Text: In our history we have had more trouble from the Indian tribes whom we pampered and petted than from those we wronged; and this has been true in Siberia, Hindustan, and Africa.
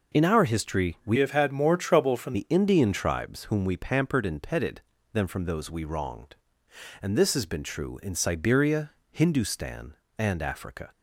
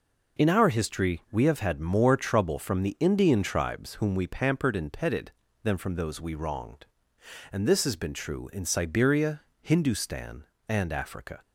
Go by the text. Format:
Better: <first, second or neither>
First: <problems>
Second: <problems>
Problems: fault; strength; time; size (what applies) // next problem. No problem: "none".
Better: second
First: changes voice from "have" to "from"; from 1.1 to 2.3 s; 1.2 s long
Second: none